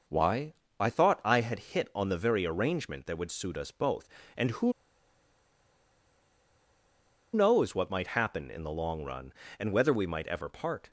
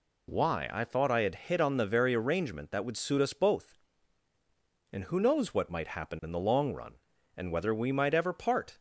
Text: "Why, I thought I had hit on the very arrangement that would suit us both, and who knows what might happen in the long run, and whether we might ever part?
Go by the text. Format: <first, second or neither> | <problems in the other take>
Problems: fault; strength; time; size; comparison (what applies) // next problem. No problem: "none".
second | pauses between "who" and "knows"; strong; at 4.7 s; 2.6 s long